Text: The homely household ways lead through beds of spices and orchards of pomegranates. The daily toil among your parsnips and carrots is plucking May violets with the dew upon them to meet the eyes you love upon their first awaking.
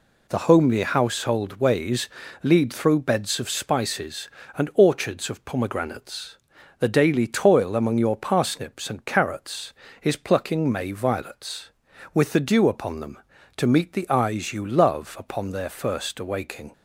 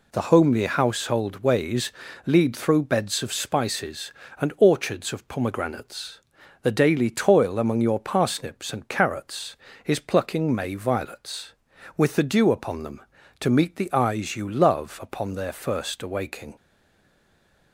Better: first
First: pauses between "ways" and "lead"; slight; at 2.0 s; 0.36 s long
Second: pauses between "ways" and "lead"; slight; at 1.9 s; 0.36 s long // stays silent after the last word; noticeable; from 16.5 s on; 1.2 s long

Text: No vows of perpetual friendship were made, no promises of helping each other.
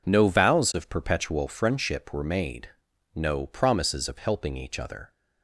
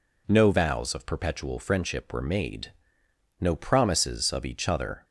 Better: first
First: none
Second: skips "helping"; at 4.4 s

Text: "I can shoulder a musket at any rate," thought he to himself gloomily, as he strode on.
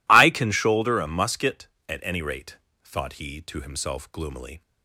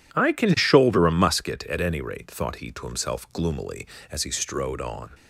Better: second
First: stops before "as he strode on"; at 4.6 s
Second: none

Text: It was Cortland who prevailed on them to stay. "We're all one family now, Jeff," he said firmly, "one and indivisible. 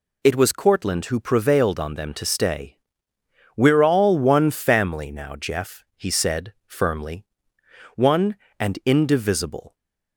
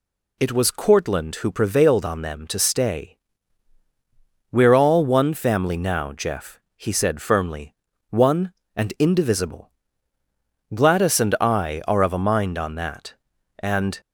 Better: first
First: none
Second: goes on to say "Gladys and I are of a mind on that and"; strong; from 10.7 s on; 3.2 s long

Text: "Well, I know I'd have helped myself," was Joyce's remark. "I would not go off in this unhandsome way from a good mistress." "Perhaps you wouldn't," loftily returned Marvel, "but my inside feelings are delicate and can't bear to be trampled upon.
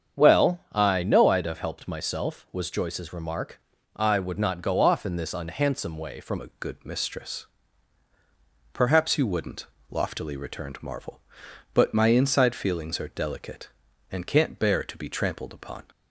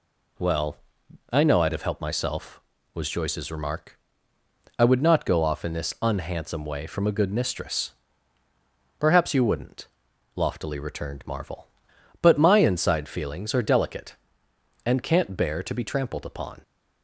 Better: second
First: starts louder than the rest; strong; until 1.2 s; 7.5 dB // changes voice at "a"; from 6.4 s on; 9.4 s long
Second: none

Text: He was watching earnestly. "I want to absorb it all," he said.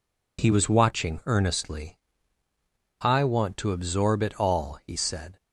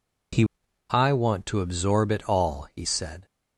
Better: first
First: none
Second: skips "was watching earnestly"; at 0.6 s

